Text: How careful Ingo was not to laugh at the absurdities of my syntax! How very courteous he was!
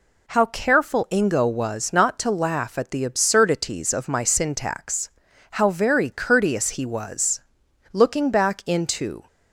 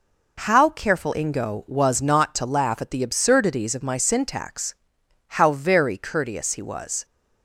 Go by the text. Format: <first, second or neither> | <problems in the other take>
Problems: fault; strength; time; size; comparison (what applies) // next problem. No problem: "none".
second | goes on to say "Looking back into"; from 7.9 s on; 1.3 s long